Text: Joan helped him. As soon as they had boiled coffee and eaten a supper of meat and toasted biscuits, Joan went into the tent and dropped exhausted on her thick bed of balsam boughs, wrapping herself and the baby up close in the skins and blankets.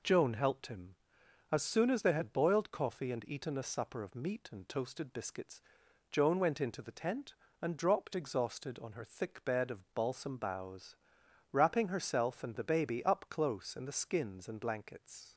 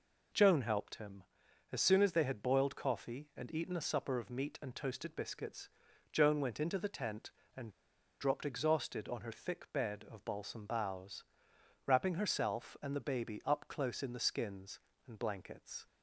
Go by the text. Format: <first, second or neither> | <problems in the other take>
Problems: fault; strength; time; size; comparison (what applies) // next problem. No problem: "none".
first | pauses between "and" and "dropped"; noticeable; at 7.6 s; 0.50 s long